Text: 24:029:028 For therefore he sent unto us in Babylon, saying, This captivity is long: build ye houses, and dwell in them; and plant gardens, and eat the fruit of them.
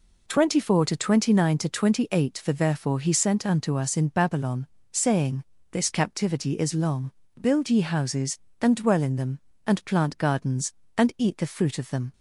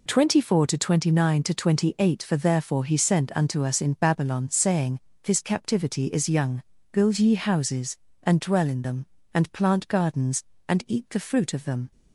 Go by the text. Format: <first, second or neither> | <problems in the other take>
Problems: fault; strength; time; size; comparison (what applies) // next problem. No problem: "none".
first | says "young" for "long"; at 6.2 s